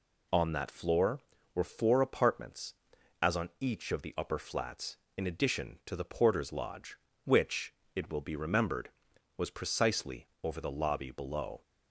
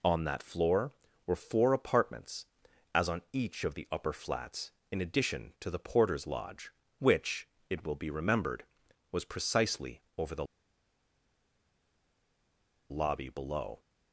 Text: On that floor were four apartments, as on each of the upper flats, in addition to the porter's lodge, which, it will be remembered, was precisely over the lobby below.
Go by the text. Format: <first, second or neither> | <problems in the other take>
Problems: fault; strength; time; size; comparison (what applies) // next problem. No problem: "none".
first | pauses between "precisely" and "over"; slight; at 10.0 s; 0.16 s long; slight in the first // pauses between "the" and "lobby"; strong; at 10.4 s; 2.4 s long